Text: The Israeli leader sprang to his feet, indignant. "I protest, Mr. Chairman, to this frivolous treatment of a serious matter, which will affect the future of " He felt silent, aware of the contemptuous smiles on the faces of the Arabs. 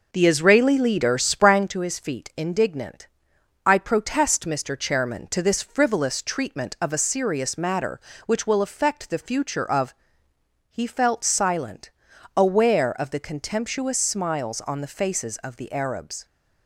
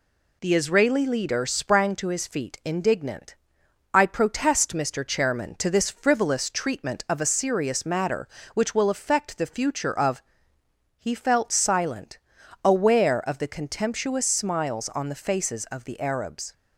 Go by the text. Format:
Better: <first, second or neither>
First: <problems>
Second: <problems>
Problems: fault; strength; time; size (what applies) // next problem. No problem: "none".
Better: second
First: starts louder than the rest; noticeable; until 1.7 s; 5.5 dB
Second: none